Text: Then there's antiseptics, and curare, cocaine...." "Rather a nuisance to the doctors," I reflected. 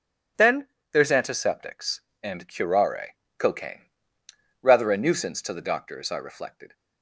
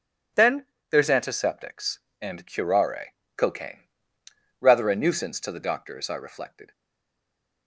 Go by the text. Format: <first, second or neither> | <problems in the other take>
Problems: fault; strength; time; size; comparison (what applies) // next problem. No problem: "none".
first | pauses between "Then" and "there's"; slight; at 0.6 s; 0.24 s long; slight in the first // stays silent after the last word; from 6.7 s on; 0.9 s long